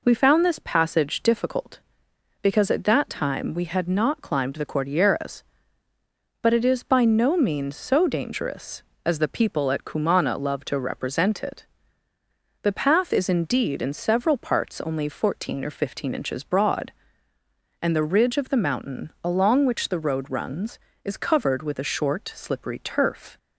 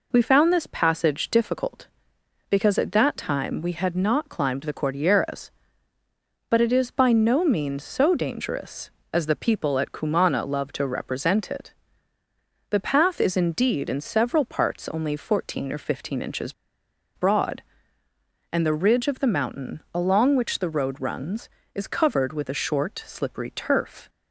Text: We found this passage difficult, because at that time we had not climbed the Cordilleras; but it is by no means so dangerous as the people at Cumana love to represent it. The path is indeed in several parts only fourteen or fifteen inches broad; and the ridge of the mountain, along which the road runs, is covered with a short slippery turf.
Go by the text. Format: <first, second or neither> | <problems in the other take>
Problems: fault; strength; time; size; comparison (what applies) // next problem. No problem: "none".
first | pauses between "inches" and "broad"; noticeable; at 16.5 s; 0.63 s long